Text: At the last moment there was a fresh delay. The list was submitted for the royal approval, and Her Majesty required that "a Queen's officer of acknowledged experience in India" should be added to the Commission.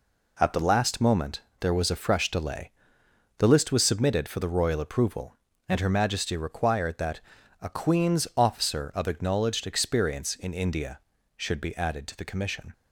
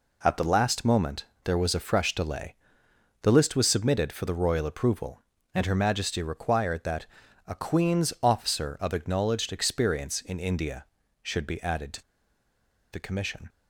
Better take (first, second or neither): first